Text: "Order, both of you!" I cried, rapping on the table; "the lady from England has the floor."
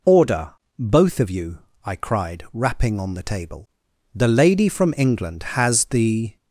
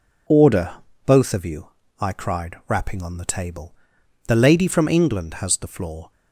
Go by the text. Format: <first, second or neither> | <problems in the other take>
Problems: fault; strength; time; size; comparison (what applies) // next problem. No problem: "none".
second | stops before "floor"; at 6.3 s